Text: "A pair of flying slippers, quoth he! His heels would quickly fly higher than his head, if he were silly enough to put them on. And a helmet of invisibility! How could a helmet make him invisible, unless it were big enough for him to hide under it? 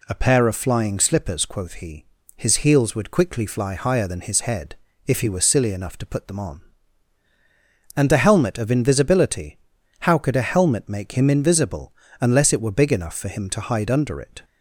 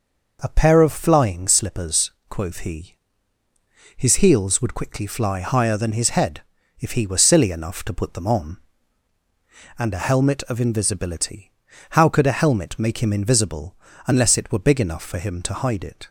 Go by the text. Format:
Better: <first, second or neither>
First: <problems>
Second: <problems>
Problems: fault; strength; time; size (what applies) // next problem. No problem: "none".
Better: first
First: none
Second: skips "under"; at 15.8 s